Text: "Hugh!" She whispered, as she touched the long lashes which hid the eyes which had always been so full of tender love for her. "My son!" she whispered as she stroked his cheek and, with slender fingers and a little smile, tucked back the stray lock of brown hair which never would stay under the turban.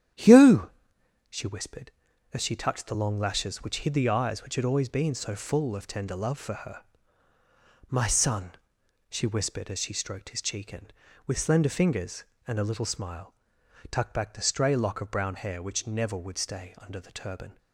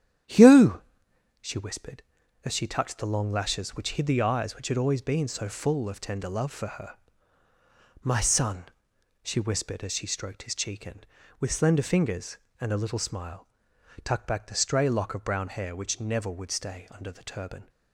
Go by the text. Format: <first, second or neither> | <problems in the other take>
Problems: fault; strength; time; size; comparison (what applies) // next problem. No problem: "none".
neither | starts louder than the rest; strong; the same in both